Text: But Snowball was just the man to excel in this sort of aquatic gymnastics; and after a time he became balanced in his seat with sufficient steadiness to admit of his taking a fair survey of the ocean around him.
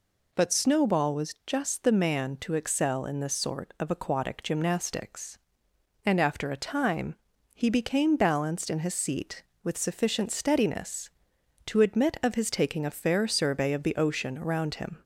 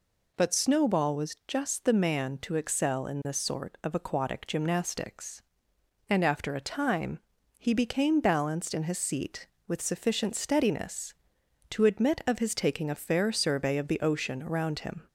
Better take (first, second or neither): neither